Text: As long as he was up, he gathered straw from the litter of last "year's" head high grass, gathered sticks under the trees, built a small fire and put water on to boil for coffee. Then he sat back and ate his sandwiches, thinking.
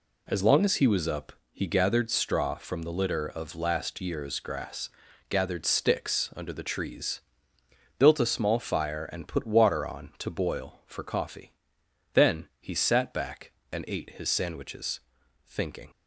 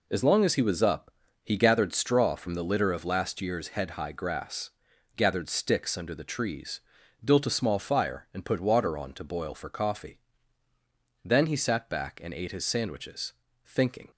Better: second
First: skips "head high"; at 4.4 s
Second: none

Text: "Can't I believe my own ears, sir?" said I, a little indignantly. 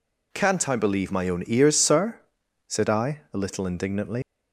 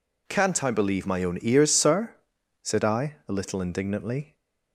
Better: second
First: leaves "indignantly" unfinished; at 4.2 s; 185 ms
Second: none

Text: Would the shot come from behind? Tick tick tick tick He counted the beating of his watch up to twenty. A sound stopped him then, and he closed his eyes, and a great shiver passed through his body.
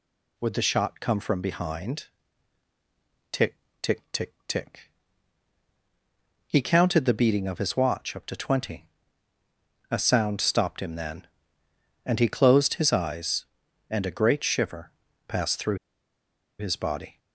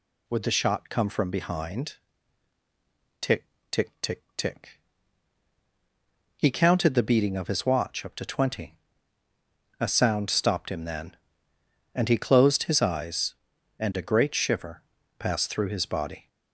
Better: second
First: pauses between "Tick" and "tick"; slight; at 3.5 s; 0.24 s long // pauses between "tick" and "He"; strong; at 4.9 s; 1.5 s long // pauses between "shiver" and "passed"; slight; at 14.9 s; 0.36 s long // pauses between "through" and "his"; noticeable; at 15.7 s; 0.82 s long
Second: pauses between "Tick" and "tick"; slight; at 3.4 s; 0.24 s long // pauses between "tick" and "He"; strong; at 4.7 s; 1.5 s long // pauses between "shiver" and "passed"; slight; at 14.8 s; 0.36 s long

